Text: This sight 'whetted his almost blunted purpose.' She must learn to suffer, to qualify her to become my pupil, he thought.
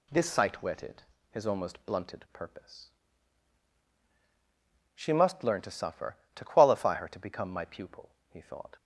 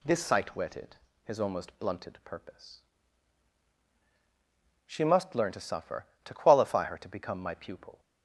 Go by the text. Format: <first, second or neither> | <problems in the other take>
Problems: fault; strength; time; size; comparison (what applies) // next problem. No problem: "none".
first | pauses between "whetted" and "his"; slight; at 0.9 s; 0.30 s long; slight in the first // stops before "he thought"; at 7.9 s